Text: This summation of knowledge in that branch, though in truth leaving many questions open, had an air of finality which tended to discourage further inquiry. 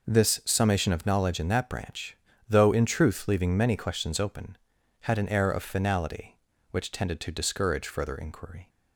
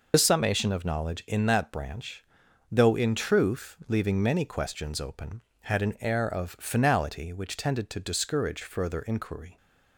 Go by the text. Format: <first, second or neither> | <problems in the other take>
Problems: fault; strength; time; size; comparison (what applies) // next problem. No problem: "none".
first | loses the start of "This"; at 0.1 s; 75 ms